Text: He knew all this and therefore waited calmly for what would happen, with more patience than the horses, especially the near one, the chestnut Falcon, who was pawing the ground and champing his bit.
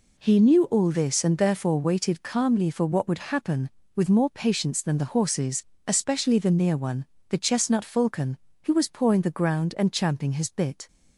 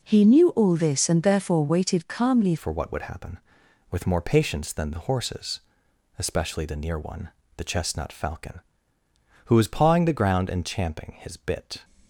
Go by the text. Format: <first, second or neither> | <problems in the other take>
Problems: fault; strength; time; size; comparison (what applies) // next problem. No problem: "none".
first | changes voice at "for"; from 2.5 s on; 9.3 s long